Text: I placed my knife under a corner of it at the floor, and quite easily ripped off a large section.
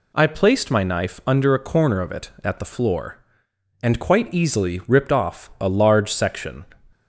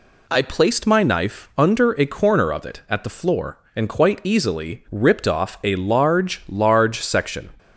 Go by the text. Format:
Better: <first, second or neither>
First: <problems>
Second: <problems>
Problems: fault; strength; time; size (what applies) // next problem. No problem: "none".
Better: first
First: none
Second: says "large" twice; at 6.4 s